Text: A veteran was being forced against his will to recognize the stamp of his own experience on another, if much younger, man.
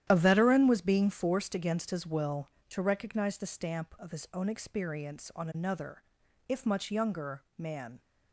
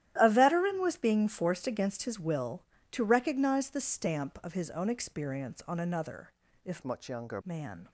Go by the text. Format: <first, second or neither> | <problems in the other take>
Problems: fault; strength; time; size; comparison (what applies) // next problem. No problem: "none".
first | starts louder than the rest; strong; until 1.1 s; 12.5 dB; strong in the first // changes voice from "much" to "younger"; from 6.8 to 7.4 s; 0.6 s long